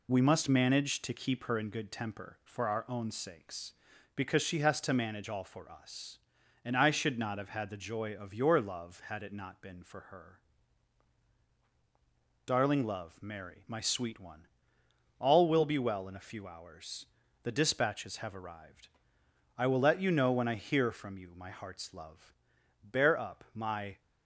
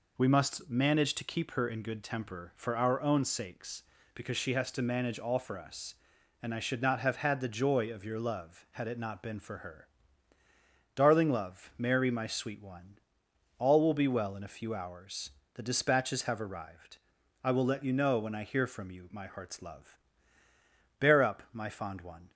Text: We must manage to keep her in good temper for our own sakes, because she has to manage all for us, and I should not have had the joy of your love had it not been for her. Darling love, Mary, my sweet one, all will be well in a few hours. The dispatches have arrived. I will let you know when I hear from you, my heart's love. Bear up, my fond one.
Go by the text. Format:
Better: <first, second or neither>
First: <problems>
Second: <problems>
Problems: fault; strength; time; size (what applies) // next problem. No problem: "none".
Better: second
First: stops before "fond one"; at 23.9 s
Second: none